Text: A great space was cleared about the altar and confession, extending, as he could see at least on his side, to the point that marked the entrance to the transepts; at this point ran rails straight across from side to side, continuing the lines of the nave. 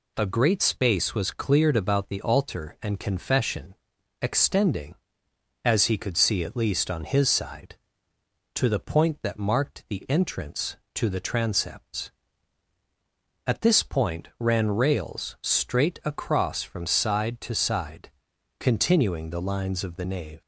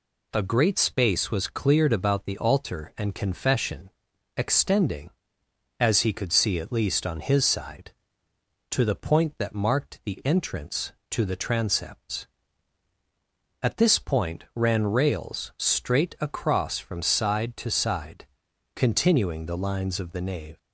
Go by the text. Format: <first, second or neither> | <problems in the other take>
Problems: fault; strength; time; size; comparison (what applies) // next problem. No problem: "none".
neither | none